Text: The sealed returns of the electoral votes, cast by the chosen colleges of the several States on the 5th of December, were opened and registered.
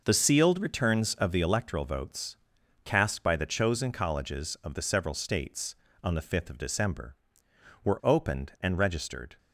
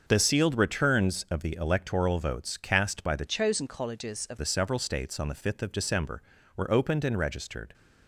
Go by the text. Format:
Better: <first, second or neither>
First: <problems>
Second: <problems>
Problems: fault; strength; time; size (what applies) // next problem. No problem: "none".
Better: first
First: none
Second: starts louder than the rest; until 1.0 s; 6.5 dB // changes voice from "chosen" to "of"; from 3.2 to 4.3 s; 1.1 s long